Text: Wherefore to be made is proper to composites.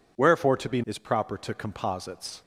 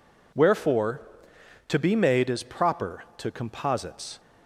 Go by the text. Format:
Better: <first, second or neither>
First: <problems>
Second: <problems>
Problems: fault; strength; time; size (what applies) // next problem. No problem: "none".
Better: second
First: skips "made"; at 0.8 s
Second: none